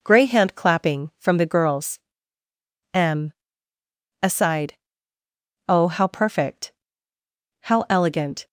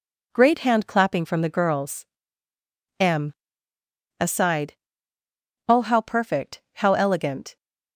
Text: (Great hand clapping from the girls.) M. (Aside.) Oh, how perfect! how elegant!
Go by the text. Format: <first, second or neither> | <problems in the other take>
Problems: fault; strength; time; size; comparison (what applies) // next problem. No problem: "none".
second | says "Grey" for "Great"; at 0.0 s